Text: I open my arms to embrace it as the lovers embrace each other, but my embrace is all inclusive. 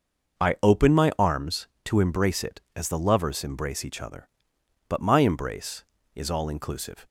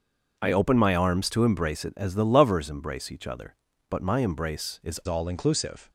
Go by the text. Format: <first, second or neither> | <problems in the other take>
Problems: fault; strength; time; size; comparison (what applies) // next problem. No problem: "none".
first | starts louder than the rest; noticeable; until 1.4 s; 6 dB // changes voice at "all"; from 5.0 s on; 0.9 s long